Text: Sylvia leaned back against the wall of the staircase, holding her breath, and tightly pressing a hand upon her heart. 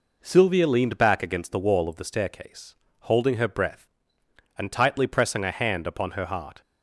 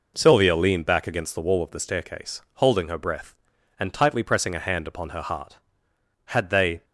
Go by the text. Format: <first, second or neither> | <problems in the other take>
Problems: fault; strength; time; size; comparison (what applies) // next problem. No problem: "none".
first | goes on to say "Had they"; from 6.2 s on; 0.58 s long